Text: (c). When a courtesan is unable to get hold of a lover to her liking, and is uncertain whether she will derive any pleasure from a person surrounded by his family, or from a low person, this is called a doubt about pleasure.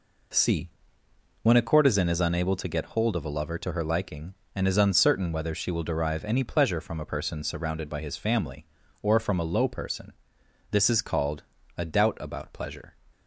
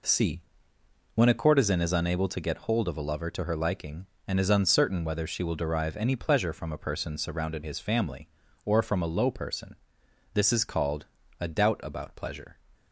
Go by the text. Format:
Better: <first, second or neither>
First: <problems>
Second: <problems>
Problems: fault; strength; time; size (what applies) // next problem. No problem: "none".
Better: first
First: pauses between "called" and "a"; slight; at 11.4 s; 0.34 s long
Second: skips "by"; at 7.6 s // pauses between "called" and "a"; slight; at 11.0 s; 0.34 s long